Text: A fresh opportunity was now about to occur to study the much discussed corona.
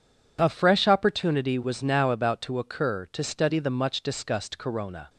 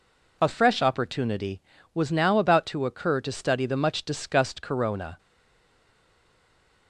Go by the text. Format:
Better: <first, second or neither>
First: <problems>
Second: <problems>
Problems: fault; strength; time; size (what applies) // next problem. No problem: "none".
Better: first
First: none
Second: stays silent after the last word; noticeable; from 5.1 s on; 1.7 s long